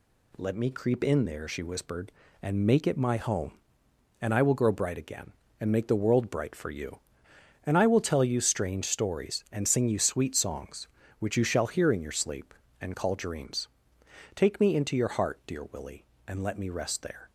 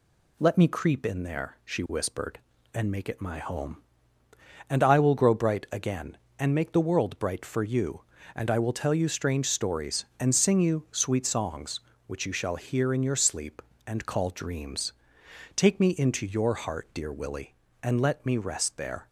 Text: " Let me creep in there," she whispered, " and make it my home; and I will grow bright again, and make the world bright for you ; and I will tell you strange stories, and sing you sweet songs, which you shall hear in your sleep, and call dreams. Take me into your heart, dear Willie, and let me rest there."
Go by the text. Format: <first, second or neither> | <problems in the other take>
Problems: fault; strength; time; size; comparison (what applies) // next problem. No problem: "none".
neither | none